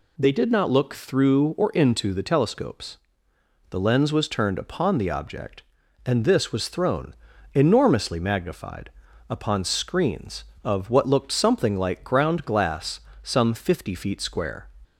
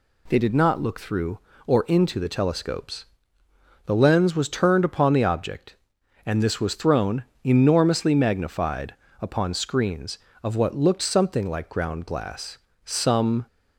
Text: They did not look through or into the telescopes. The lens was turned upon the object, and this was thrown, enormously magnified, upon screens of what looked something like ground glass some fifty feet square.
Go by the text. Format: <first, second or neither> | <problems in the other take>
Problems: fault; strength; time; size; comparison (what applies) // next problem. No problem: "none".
first | pauses between "glass" and "some"; slight; at 12.5 s; 0.26 s long; slight in the first // stops before "fifty feet square"; at 13.4 s